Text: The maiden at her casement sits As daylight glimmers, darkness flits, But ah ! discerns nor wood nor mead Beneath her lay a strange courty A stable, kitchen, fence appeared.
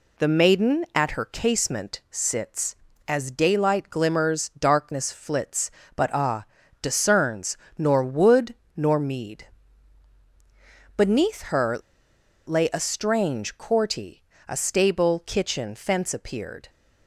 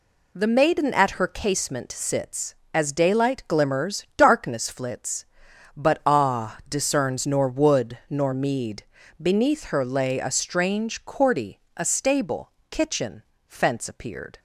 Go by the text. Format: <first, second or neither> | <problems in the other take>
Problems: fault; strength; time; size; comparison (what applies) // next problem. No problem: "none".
second | pauses between "discerns" and "nor"; slight; at 7.5 s; 0.20 s long // pauses between "wood" and "nor"; slight; at 8.5 s; 0.22 s long // pauses between "mead" and "Beneath"; strong; at 9.4 s; 1.4 s long; slight in the second // pauses between "her" and "lay"; noticeable; at 11.7 s; 0.68 s long // pauses between "courty" and "A"; slight; at 14.2 s; 0.24 s long; slight in the second